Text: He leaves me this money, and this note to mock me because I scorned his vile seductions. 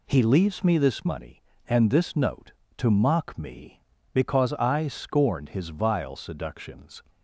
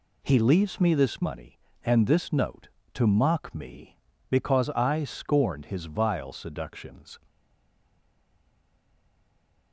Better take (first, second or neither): first